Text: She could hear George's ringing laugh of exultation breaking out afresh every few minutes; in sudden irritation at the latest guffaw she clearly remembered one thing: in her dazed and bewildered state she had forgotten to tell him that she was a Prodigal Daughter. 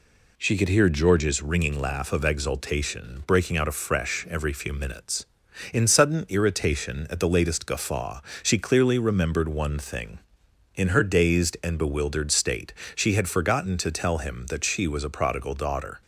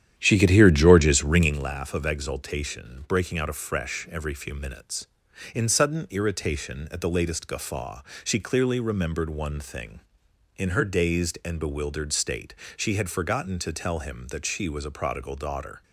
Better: first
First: pauses between "guffaw" and "she"; slight; at 8.1 s; 0.24 s long // pauses between "state" and "she"; slight; at 12.7 s; 0.22 s long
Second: starts louder than the rest; strong; until 1.7 s; 10 dB // pauses between "guffaw" and "she"; slight; at 8.0 s; 0.24 s long // pauses between "state" and "she"; slight; at 12.5 s; 0.22 s long

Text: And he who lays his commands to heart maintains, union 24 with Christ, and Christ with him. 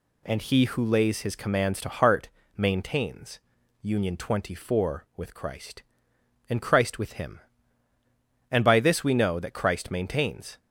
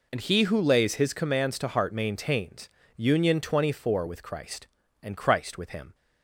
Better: second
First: pauses between "heart" and "maintains"; slight; at 2.2 s; 0.28 s long // goes on to say "And by this we know that Christ maintains"; strong; from 8.5 s on; 2.0 s long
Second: none

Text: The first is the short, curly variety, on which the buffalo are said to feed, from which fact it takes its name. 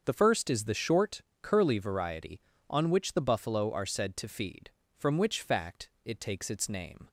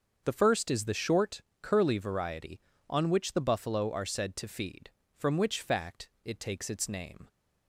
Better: neither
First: starts louder than the rest; until 1.0 s; 6.5 dB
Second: starts louder than the rest; until 1.2 s; 6.5 dB

